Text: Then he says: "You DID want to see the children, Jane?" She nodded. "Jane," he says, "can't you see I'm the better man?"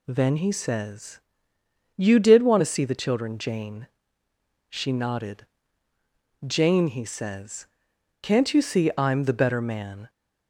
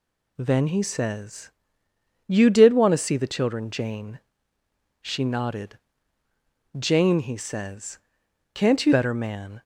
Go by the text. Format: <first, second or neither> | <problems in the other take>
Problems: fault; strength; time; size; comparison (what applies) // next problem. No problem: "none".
first | skips "see I'm the"; at 8.9 s